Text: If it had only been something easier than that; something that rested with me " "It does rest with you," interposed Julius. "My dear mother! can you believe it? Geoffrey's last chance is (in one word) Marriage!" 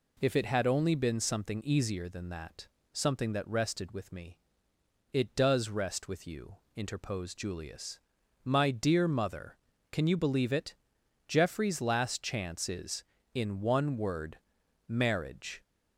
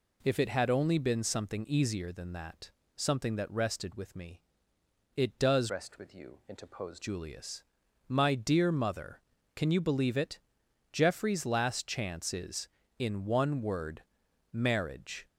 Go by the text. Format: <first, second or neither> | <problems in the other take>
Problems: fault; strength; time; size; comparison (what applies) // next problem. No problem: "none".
first | changes voice from "rest" to "interposed"; from 5.6 to 7.0 s; 1.4 s long